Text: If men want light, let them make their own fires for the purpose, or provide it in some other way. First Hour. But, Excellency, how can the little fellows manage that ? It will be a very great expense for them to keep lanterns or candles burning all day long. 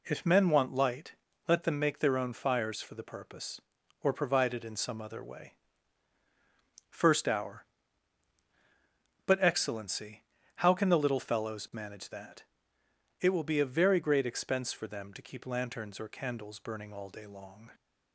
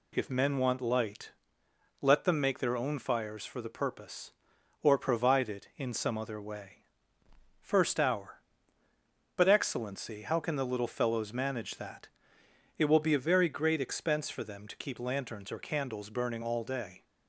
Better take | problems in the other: first | stops before "long"; at 17.0 s

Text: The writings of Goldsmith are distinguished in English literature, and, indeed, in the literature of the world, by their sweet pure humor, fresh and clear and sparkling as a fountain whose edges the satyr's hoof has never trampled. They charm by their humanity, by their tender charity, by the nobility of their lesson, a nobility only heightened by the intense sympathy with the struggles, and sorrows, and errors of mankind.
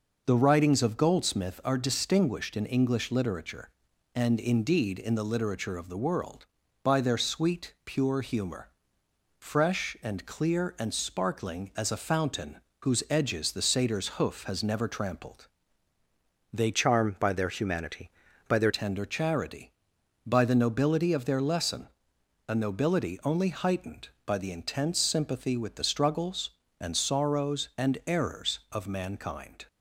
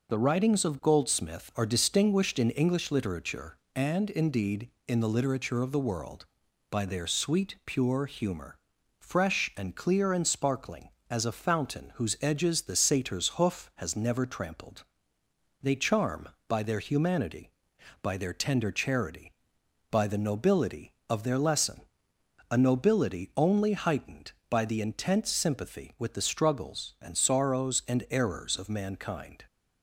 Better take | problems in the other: second | pauses between "fountain" and "whose"; slight; at 12.5 s; 0.20 s long // changes voice from "charm" to "their"; from 16.7 to 18.7 s; 2.0 s long

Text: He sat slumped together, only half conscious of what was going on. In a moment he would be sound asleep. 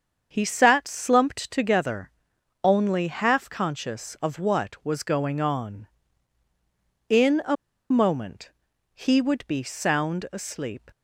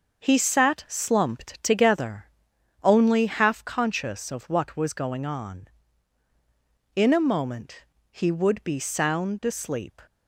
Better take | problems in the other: second | starts louder than the rest; until 1.3 s; 7 dB; also in the second // pauses between "a" and "moment"; slight; at 7.5 s; 0.35 s long // pauses between "moment" and "he"; noticeable; at 8.4 s; 0.46 s long; slight in the second

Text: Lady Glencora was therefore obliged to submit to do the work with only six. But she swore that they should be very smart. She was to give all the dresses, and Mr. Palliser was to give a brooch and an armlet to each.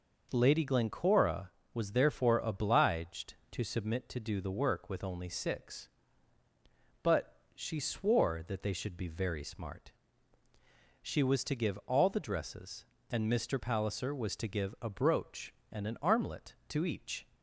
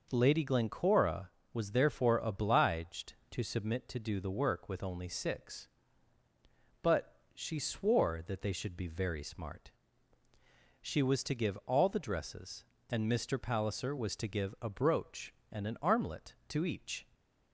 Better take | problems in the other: neither | pauses between "But" and "she"; slight; the same in both

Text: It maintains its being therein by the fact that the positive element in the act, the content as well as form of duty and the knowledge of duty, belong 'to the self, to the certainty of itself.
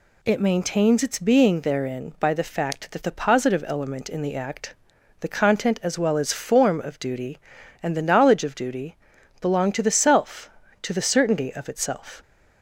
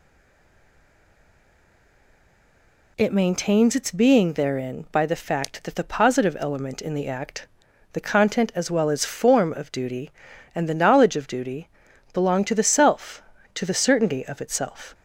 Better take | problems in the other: first | stays silent before the first word; strong; until 2.9 s; 2.9 s long

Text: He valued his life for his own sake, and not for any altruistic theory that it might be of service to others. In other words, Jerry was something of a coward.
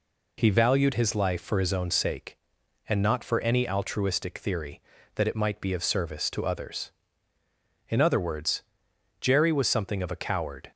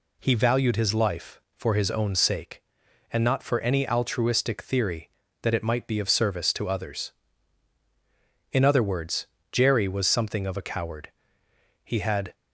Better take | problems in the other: first | goes on to say "He had"; from 11.8 s on; 0.50 s long

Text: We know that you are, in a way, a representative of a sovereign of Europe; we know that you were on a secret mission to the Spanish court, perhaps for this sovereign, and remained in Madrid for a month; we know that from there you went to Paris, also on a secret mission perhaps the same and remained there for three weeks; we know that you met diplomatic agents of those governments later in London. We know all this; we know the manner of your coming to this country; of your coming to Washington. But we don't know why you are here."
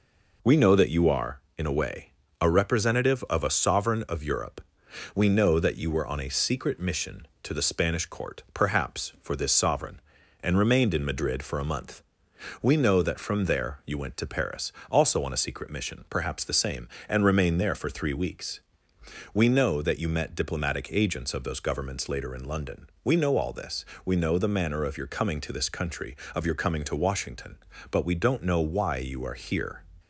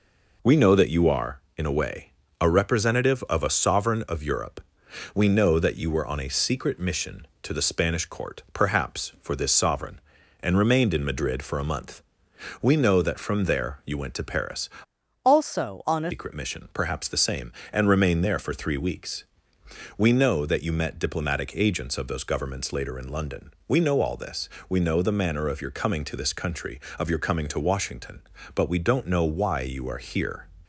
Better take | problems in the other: first | changes voice from "also" to "a"; from 15.2 to 16.1 s; 0.9 s long

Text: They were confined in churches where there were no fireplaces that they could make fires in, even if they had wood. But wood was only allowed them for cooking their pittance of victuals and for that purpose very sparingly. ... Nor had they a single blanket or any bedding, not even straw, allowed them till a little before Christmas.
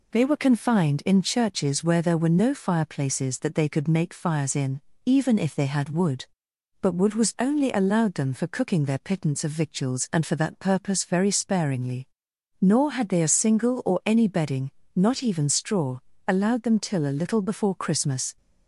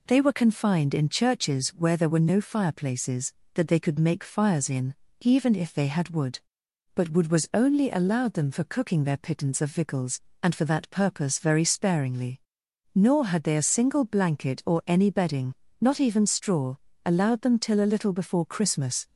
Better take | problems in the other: second | skips "blanket"; at 13.8 s

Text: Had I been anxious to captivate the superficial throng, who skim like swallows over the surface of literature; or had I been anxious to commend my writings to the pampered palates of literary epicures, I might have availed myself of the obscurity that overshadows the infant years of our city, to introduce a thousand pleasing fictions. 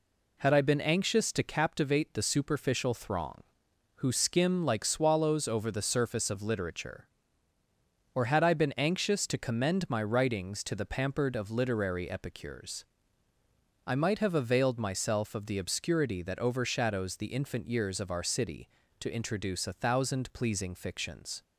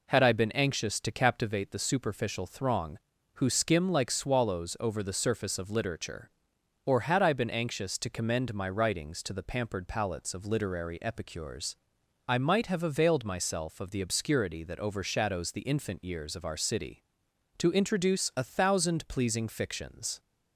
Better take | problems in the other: second | skips "palates"; at 11.3 s

